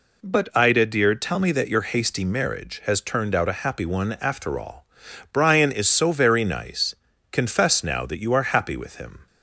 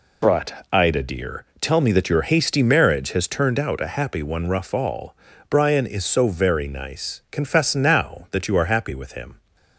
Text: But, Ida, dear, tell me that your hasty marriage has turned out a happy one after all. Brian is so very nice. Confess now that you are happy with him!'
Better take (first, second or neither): first